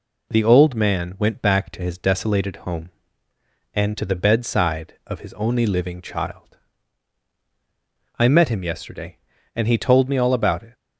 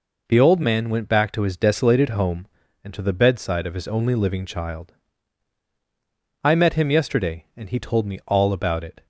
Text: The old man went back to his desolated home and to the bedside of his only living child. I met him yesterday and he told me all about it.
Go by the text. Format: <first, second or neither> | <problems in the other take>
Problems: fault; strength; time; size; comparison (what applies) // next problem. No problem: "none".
neither | none